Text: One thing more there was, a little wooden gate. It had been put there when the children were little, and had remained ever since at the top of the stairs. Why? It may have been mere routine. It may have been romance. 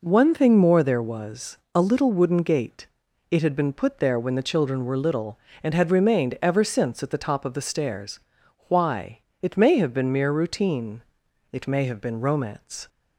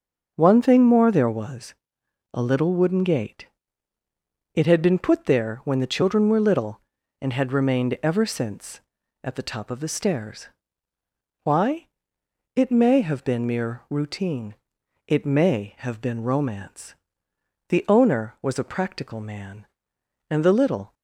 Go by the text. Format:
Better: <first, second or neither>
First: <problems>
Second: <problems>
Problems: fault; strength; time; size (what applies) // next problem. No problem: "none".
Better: first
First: none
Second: starts louder than the rest; until 1.3 s; 6 dB // goes on to say "The Owner was a practical man and the little"; strong; from 17.6 s on; 3.2 s long